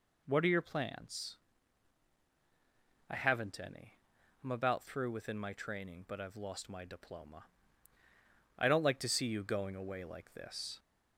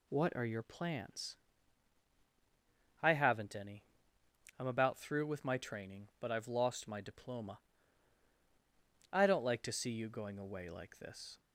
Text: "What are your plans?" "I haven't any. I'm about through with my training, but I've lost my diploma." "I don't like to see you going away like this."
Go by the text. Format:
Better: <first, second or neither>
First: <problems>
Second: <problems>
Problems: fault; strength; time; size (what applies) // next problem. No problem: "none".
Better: second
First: says "within" for "with"; at 5.1 s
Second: none